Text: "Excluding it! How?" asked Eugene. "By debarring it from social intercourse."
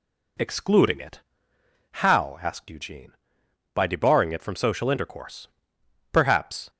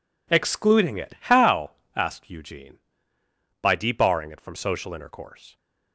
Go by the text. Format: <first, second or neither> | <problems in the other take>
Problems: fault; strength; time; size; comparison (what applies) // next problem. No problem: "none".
second | goes on to say "Perhaps"; from 6.1 s on; 0.58 s long